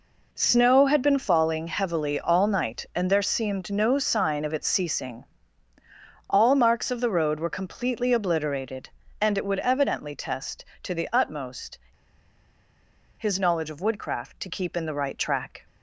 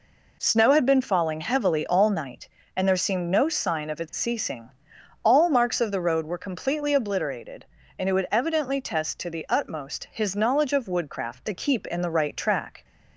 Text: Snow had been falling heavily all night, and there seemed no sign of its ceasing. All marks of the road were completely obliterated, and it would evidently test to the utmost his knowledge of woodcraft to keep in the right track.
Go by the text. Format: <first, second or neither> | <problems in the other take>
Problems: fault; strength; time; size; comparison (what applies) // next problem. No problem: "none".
second | pauses between "utmost" and "his"; strong; at 11.7 s; 1.4 s long